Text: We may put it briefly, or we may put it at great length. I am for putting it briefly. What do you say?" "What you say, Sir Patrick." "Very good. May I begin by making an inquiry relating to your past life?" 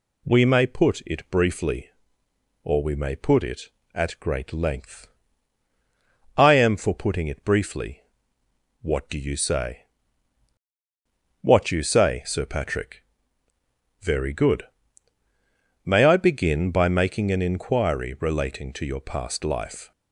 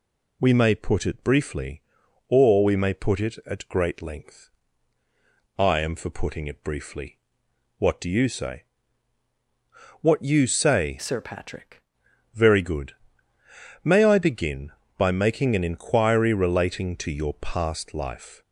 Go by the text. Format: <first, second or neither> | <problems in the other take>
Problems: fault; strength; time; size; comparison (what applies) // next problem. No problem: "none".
first | changes voice from "Sir" to "Patrick"; from 10.9 to 11.8 s; 0.9 s long